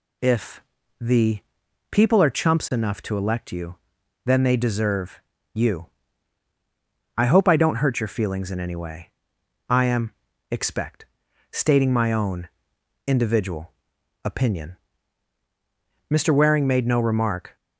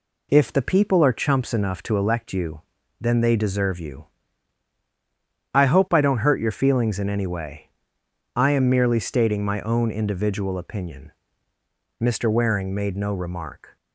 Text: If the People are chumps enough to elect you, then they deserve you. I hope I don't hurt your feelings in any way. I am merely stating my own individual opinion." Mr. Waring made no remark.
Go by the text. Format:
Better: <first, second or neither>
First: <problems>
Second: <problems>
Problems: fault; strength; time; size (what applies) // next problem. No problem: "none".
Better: second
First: pauses between "If" and "the"; slight; at 0.6 s; 0.36 s long // pauses between "the" and "People"; noticeable; at 1.3 s; 0.50 s long // pauses between "deserve" and "you"; slight; at 5.1 s; 0.34 s long // says "expect" for "merely"; at 10.5 s // pauses between "own" and "individual"; noticeable; at 12.4 s; 0.60 s long // pauses between "individual" and "opinion"; noticeable; at 13.7 s; 0.52 s long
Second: none